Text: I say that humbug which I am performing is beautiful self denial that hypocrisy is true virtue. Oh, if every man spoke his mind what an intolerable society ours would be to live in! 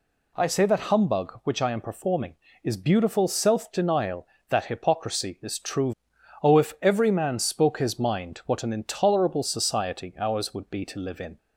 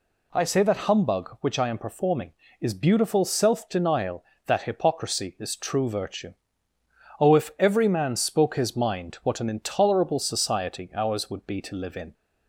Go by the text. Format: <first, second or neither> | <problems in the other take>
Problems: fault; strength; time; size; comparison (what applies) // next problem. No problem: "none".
second | skips "virtue"; at 6.1 s